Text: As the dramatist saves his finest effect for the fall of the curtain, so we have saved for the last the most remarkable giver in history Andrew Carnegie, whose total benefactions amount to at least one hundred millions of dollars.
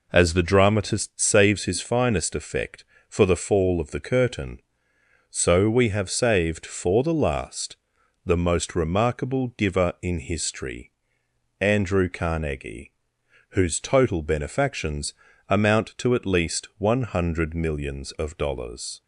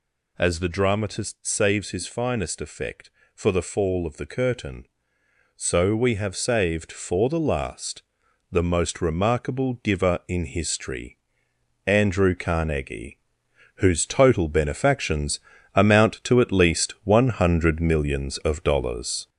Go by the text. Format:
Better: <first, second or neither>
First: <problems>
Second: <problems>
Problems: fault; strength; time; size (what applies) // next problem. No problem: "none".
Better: first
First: pauses between "last" and "the"; noticeable; at 7.7 s; 0.48 s long // pauses between "history" and "Andrew"; noticeable; at 10.9 s; 0.68 s long // pauses between "benefactions" and "amount"; slight; at 15.1 s; 0.34 s long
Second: gets louder; noticeable; throughout; 5.5 dB // pauses between "last" and "the"; noticeable; at 8.0 s; 0.48 s long // pauses between "history" and "Andrew"; noticeable; at 11.1 s; 0.68 s long // pauses between "benefactions" and "amount"; slight; at 15.3 s; 0.34 s long